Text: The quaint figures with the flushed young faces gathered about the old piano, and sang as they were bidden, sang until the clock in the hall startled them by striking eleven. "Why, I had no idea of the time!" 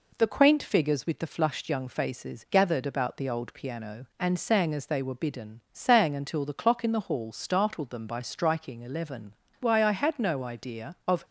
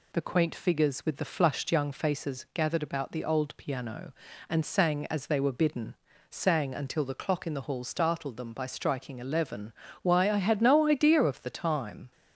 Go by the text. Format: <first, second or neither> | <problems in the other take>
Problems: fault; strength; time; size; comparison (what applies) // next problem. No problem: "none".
second | stops before "the time"; at 11.2 s